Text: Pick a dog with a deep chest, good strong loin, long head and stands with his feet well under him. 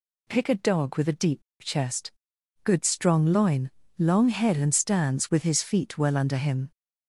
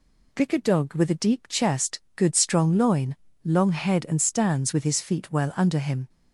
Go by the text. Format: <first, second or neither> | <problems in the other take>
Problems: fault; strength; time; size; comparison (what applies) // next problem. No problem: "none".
second | pauses between "deep" and "chest"; slight; at 1.4 s; 0.20 s long